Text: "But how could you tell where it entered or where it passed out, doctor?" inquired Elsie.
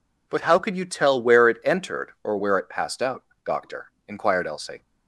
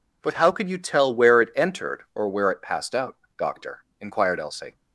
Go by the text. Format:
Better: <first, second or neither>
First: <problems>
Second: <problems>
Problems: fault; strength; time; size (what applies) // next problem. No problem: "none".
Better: neither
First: none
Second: none